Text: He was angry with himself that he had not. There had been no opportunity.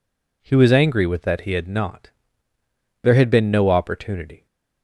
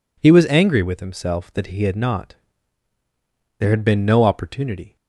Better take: second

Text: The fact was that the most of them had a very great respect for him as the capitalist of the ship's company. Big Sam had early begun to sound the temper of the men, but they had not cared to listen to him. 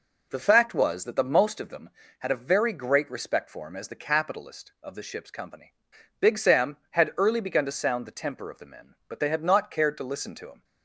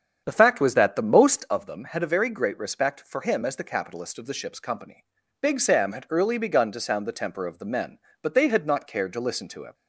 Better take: first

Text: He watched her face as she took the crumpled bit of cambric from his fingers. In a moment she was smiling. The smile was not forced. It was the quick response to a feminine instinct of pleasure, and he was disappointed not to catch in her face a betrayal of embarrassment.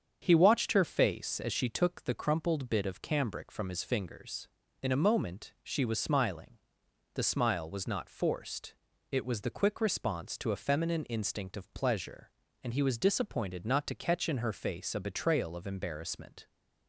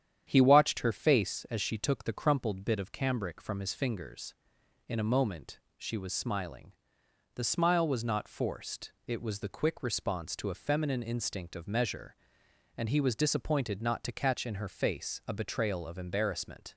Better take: first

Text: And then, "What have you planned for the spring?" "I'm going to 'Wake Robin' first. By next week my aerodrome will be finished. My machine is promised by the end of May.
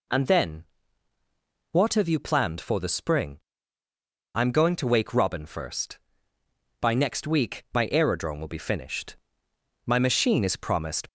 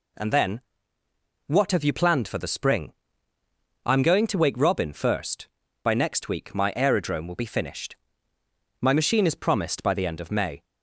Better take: second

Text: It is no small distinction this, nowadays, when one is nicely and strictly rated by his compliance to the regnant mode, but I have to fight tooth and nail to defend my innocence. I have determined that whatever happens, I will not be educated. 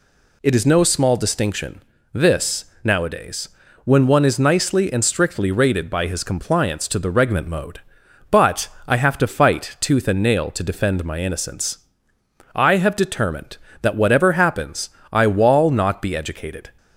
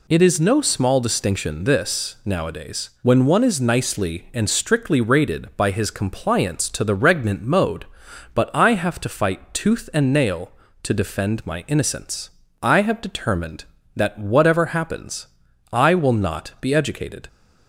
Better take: second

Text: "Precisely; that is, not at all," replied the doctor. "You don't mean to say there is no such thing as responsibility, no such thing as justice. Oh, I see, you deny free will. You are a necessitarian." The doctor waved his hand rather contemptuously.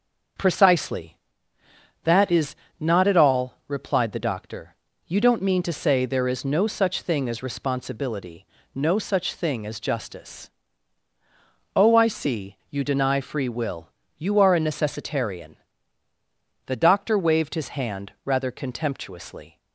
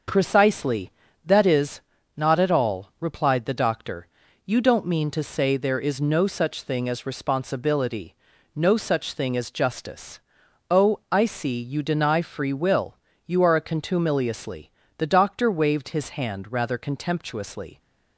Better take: first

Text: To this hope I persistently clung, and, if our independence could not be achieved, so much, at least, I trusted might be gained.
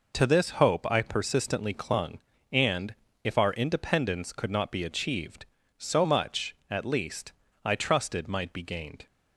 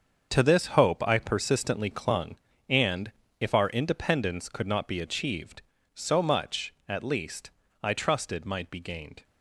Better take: first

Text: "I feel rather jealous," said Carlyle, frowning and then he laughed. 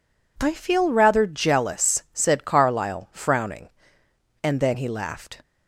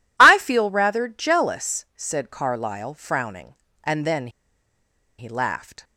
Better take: first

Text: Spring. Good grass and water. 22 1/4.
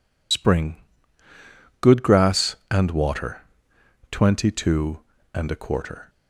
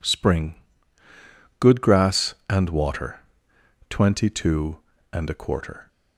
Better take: second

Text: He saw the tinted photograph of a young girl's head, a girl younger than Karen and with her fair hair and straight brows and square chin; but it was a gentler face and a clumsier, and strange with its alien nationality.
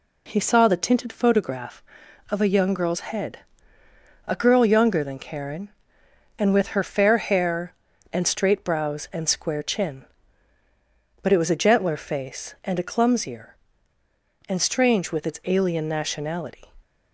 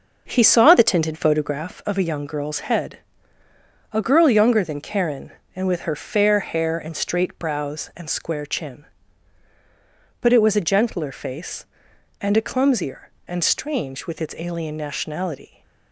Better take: first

